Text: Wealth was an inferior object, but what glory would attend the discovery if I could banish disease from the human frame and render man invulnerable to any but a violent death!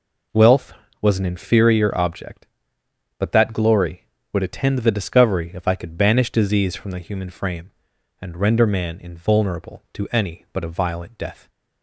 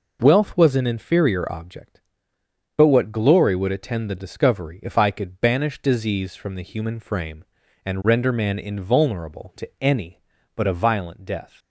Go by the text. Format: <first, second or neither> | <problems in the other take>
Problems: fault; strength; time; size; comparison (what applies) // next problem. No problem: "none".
second | says "that" for "what"; at 3.3 s